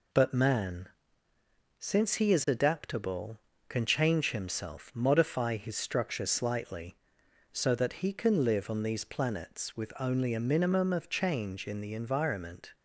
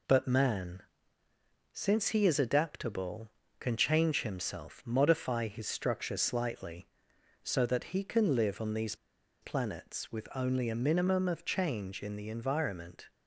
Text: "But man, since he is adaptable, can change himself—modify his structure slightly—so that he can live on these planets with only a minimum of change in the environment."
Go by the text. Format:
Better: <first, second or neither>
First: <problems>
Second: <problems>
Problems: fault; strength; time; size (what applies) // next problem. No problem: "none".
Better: first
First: none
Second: pauses between "these" and "planets"; noticeable; at 8.9 s; 0.47 s long